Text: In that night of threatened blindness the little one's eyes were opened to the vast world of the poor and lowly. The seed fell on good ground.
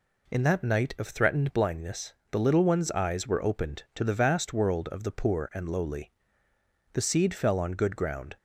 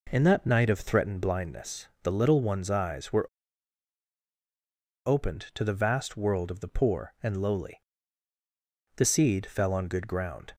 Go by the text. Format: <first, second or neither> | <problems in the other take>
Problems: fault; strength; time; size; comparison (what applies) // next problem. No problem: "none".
first | pauses between "blindness" and "the"; slight; at 1.8 s; 0.16 s long; slight in the first // pauses between "were" and "opened"; strong; at 3.2 s; 1.7 s long